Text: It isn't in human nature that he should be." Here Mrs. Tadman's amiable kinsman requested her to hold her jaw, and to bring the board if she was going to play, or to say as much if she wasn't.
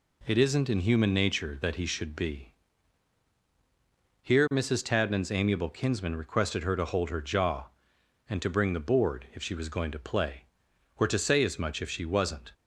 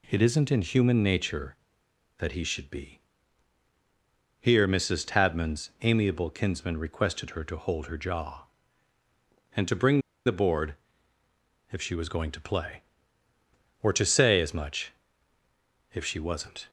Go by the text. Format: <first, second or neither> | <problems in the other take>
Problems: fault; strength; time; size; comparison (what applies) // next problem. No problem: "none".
first | pauses between "bring" and "the"; slight; at 10.0 s; 0.25 s long // pauses between "board" and "if"; noticeable; at 10.7 s; 0.96 s long // pauses between "much" and "if"; at 14.9 s; 1.0 s long